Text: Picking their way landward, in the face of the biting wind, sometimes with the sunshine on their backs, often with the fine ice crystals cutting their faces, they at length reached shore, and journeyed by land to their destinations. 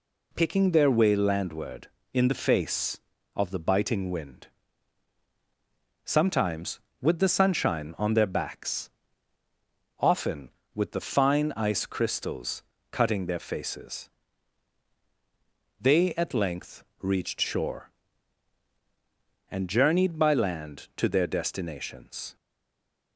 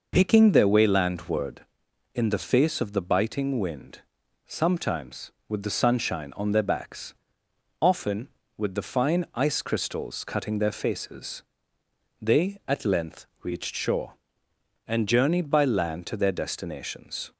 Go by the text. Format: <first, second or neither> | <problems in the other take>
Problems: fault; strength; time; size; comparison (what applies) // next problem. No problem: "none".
second | pauses between "crystals" and "cutting"; slight; at 12.6 s; 0.28 s long // pauses between "length" and "reached"; slight; at 16.8 s; 0.16 s long; slight in the second // stays silent after the last word; slight; from 22.3 s on; 0.8 s long